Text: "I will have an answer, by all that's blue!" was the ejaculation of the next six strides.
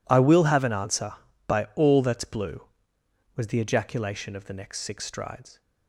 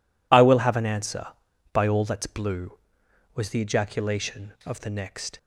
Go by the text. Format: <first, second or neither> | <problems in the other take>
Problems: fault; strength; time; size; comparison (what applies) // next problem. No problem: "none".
first | stops before "six strides"; at 5.3 s